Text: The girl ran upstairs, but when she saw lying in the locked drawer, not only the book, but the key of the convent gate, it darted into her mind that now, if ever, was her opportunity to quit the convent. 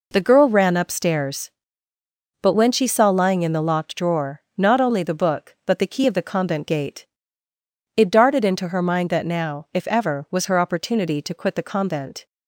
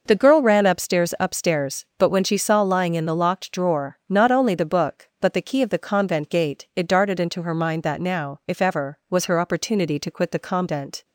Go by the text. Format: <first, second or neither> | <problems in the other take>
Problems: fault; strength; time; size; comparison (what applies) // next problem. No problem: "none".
first | says "upstairs" twice; at 1.1 s